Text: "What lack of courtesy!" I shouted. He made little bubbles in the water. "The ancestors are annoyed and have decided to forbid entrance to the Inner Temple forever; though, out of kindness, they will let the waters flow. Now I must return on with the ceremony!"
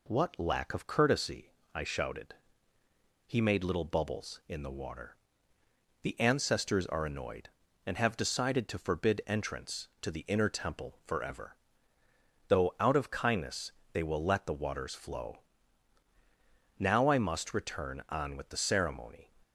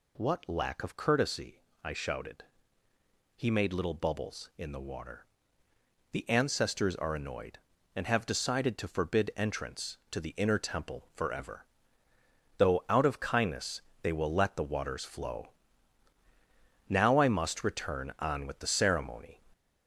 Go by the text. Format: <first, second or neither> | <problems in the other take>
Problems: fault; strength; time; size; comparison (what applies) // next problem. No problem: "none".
first | gets louder; noticeable; throughout; 4.5 dB